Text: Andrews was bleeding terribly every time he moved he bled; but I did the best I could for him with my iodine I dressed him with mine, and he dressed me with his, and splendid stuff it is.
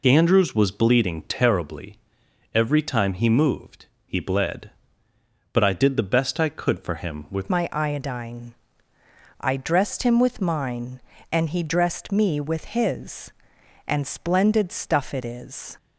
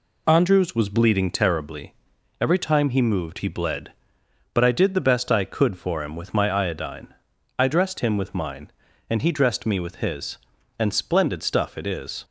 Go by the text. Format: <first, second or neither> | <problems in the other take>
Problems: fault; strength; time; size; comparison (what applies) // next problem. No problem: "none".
second | pauses between "terribly" and "every"; noticeable; at 1.9 s; 0.56 s long; noticeable in the second // pauses between "moved" and "he"; slight; at 3.8 s; 0.18 s long // changes voice at "my"; from 7.5 s on; 8.2 s long // pauses between "iodine" and "I"; noticeable; at 8.5 s; 0.84 s long; noticeable in the second